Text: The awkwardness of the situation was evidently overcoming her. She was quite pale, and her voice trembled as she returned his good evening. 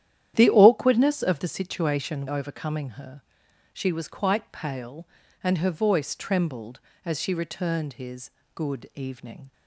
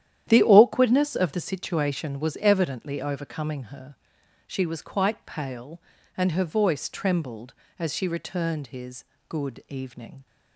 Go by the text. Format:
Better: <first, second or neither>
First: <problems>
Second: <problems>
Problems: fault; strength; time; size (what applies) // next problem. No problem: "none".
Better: second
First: starts louder than the rest; strong; until 1.3 s; 11 dB // skips "was evidently"; at 2.2 s // pauses between "his" and "good"; slight; at 8.3 s; 0.24 s long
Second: starts louder than the rest; strong; until 1.2 s; 11 dB // pauses between "his" and "good"; slight; at 9.0 s; 0.24 s long